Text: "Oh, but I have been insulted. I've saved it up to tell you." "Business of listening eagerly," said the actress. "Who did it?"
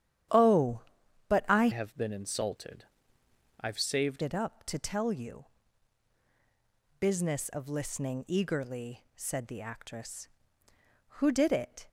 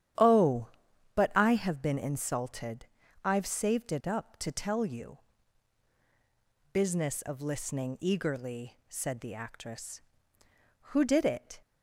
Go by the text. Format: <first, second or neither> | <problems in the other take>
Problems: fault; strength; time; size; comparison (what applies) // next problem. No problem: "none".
second | starts louder than the rest; strong; until 1.8 s; 10 dB; strong in the second // changes voice from "have" to "saved"; from 1.7 to 4.2 s; 2.5 s long